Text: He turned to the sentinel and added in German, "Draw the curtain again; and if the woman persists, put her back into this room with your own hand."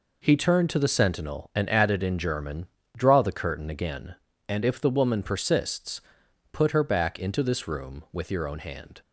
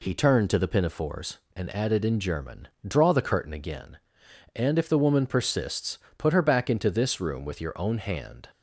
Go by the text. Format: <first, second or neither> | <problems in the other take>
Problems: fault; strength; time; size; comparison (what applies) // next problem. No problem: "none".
first | says "pinafores" for "sentinel"; at 0.6 s